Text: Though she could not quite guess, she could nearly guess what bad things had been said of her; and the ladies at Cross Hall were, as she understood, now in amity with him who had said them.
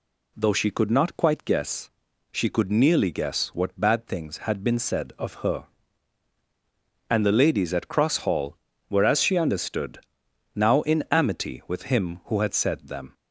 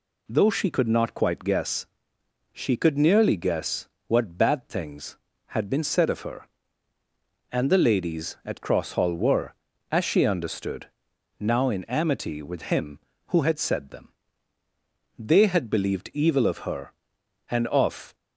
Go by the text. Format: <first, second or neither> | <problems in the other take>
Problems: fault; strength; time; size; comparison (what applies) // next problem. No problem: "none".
first | pauses between "guess" and "what"; slight; at 3.8 s; 0.18 s long // goes on to say "They had believed evil of her and of"; strong; from 15.1 s on; 2.9 s long